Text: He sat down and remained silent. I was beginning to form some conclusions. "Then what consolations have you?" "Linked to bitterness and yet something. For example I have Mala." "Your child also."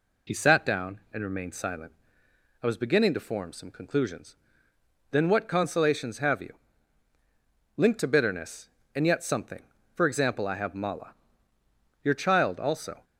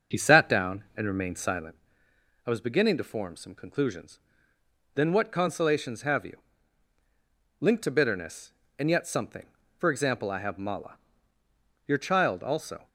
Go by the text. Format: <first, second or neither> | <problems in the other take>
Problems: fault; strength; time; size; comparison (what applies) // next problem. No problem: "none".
first | starts louder than the rest; until 1.7 s; 6.5 dB